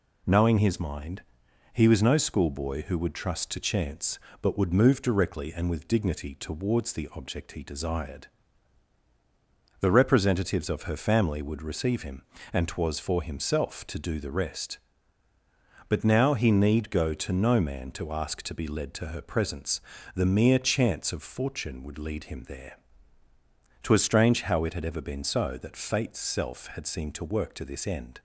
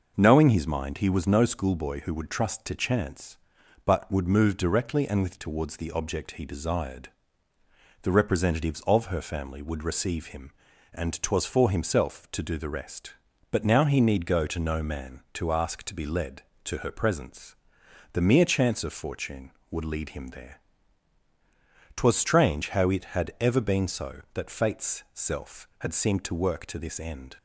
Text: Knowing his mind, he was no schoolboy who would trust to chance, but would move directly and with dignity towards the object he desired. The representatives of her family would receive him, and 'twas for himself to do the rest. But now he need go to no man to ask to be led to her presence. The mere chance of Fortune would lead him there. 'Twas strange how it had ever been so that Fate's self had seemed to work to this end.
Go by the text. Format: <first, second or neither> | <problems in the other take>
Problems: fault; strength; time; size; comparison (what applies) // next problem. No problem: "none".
first | skips "dignity"; at 5.3 s